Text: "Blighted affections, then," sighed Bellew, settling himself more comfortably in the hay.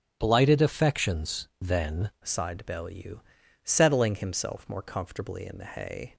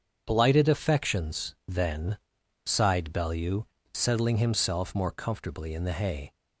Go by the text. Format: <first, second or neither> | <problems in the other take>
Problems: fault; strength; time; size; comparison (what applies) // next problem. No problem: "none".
second | starts louder than the rest; strong; until 1.2 s; 9 dB; strong in the second // changes voice at "sighed"; from 2.2 s on; 3.9 s long